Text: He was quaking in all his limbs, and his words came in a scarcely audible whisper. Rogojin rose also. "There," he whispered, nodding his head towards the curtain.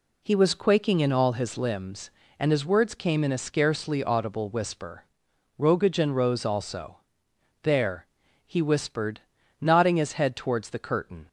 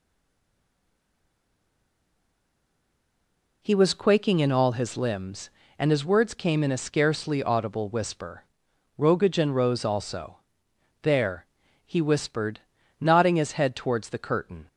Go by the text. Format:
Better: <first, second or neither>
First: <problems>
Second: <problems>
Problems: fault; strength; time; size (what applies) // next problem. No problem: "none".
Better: first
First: none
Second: stays silent before the first word; strong; until 3.6 s; 3.6 s long